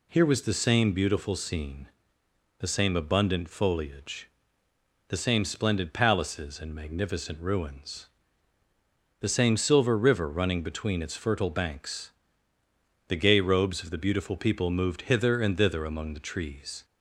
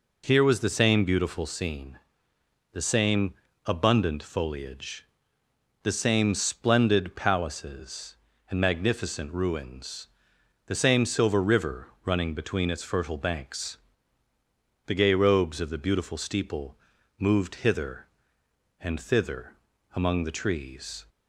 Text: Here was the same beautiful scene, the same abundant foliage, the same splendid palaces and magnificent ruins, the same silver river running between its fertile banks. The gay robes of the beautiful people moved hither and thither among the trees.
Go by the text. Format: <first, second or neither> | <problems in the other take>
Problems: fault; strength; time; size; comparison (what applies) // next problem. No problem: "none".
first | pauses between "same" and "abundant"; slight; at 3.3 s; 0.32 s long // pauses between "river" and "running"; slight; at 11.8 s; 0.18 s long // says "steeple" for "people"; at 16.1 s // pauses between "thither" and "among"; at 19.5 s; 0.40 s long